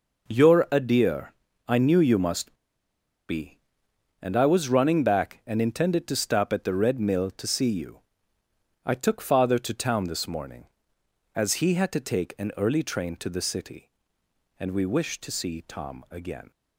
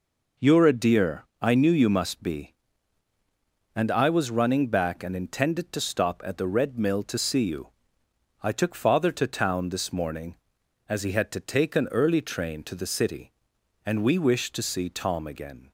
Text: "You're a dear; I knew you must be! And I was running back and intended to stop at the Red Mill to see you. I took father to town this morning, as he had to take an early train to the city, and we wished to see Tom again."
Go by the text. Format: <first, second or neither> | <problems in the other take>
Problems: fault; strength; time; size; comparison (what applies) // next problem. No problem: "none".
second | pauses between "must" and "be"; noticeable; at 2.5 s; 0.73 s long